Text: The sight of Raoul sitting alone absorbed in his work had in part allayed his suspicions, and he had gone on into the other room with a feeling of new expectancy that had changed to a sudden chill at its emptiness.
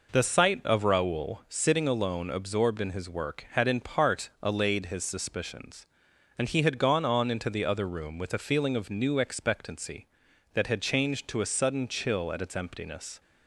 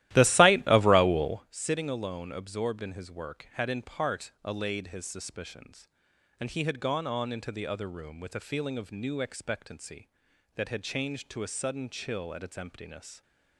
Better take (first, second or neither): first